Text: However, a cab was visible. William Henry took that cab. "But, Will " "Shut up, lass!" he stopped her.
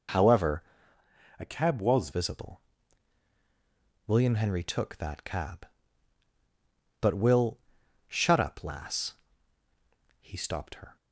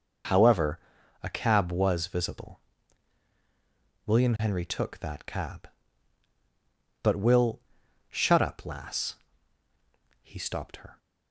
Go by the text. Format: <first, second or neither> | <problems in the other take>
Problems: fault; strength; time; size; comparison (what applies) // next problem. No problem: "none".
second | changes voice from "a" to "was"; from 1.3 to 2.0 s; 0.7 s long